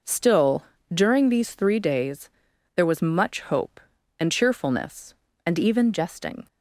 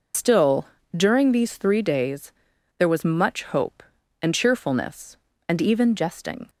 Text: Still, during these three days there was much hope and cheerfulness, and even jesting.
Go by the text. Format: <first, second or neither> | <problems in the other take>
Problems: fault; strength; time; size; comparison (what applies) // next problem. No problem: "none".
first | loses the start of "Still"; at 0.1 s; 75 ms // pauses between "days" and "there"; noticeable; at 2.3 s; 0.46 s long; noticeable in the first